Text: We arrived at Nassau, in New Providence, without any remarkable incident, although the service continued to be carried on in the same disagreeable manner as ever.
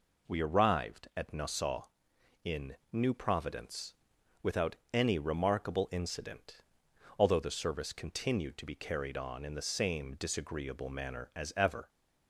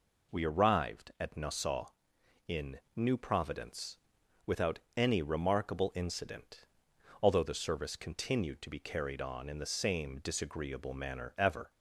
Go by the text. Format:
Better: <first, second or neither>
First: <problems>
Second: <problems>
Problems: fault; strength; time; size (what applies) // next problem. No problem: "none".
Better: first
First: pauses between "without" and "any"; slight; at 4.7 s; 0.16 s long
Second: pauses between "without" and "any"; slight; at 4.7 s; 0.16 s long // skips "as"; at 11.3 s